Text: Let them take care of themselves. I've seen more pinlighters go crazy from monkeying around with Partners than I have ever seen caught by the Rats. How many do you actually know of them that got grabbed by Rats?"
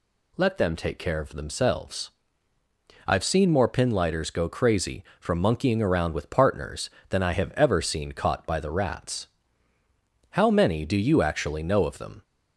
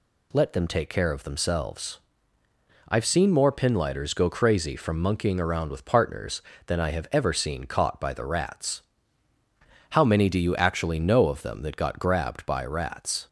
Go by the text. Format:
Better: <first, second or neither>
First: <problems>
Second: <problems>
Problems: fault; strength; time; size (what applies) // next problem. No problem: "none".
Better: second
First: stops before "that got grabbed by Rats"; at 12.2 s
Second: none